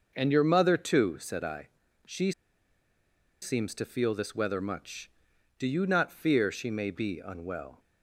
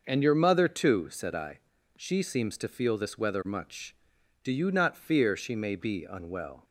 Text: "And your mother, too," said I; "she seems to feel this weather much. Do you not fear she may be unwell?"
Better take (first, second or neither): second